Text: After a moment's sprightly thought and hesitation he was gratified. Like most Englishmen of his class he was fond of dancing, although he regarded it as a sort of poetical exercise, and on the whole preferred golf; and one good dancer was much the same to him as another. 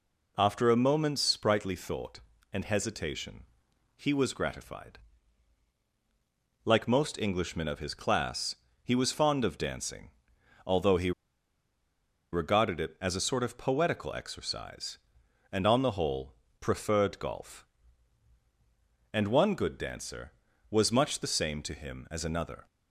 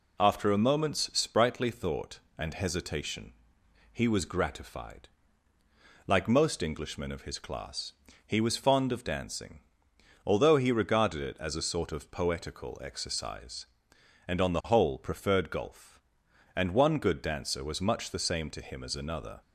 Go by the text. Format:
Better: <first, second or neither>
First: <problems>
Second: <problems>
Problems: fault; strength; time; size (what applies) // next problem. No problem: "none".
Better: second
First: pauses between "hesitation" and "he"; noticeable; at 3.4 s; 0.50 s long // pauses between "class" and "he"; slight; at 8.5 s; 0.26 s long // pauses between "he" and "regarded"; at 11.1 s; 1.2 s long // pauses between "whole" and "preferred"; slight; at 16.3 s; 0.26 s long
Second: pauses between "hesitation" and "he"; noticeable; at 3.3 s; 0.58 s long // pauses between "class" and "he"; slight; at 7.9 s; 0.32 s long